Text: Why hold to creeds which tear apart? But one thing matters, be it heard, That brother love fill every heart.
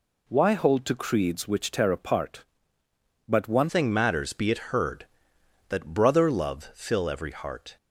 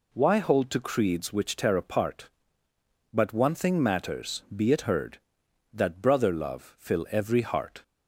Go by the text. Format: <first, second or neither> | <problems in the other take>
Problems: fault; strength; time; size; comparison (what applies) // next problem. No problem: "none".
second | changes voice at "thing"; from 3.6 s on; 4.1 s long